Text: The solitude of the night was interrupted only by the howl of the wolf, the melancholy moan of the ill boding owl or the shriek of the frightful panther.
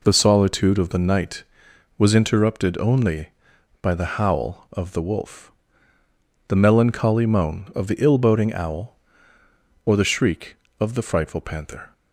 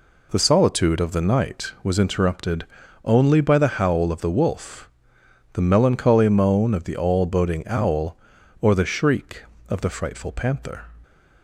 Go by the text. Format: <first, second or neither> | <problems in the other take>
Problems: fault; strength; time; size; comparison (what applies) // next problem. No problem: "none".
first | pauses between "interrupted" and "only"; at 2.6 s; 0.40 s long // says "all" for "ill"; at 6.9 s